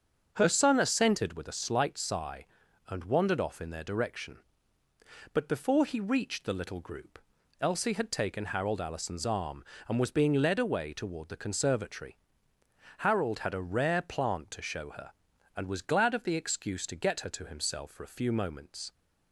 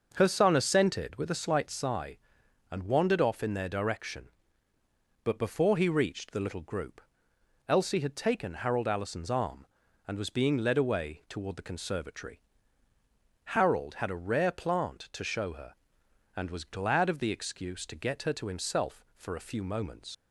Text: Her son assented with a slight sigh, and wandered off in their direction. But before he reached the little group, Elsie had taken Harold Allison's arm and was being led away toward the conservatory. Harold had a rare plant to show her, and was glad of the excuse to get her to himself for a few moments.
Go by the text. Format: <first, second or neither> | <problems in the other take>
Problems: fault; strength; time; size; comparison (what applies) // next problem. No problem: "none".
first | starts louder than the rest; noticeable; until 1.1 s; 6 dB; also in the first // leaves "moments" unfinished; at 20.1 s; 75 ms